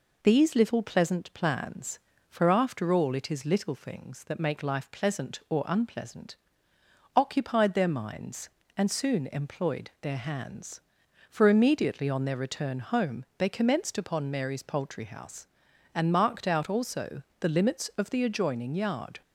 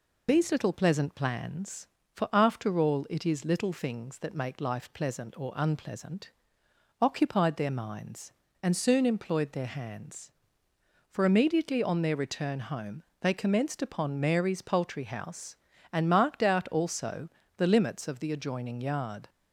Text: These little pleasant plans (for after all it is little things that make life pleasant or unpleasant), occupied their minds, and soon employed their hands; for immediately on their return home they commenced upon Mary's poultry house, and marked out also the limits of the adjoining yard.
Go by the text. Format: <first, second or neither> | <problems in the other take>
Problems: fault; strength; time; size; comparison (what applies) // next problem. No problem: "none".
first | loses the start of "These"; at 0.2 s; 45 ms // pauses between "home" and "they"; slight; at 13.0 s; 0.18 s long // pauses between "also" and "the"; slight; at 17.2 s; 0.28 s long; slight in the first